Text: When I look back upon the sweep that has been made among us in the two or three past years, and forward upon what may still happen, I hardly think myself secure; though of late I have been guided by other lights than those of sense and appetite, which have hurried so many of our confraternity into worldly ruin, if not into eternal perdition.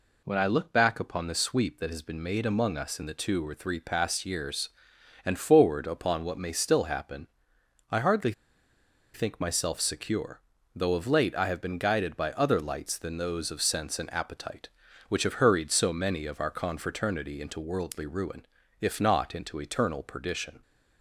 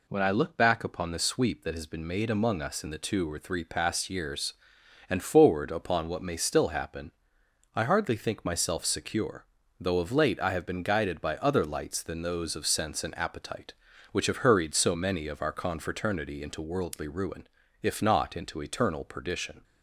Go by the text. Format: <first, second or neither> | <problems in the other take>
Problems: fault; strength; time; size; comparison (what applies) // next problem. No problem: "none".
second | pauses between "hardly" and "think"; noticeable; at 8.3 s; 0.82 s long